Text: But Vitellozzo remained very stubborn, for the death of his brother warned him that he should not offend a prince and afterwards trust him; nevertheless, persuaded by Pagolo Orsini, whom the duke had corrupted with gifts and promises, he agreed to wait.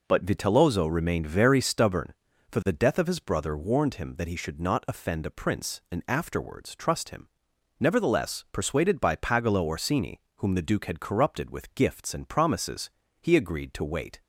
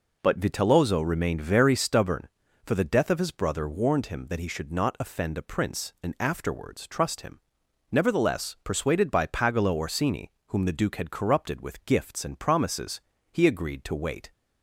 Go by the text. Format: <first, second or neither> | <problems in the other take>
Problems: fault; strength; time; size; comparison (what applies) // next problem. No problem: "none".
neither | none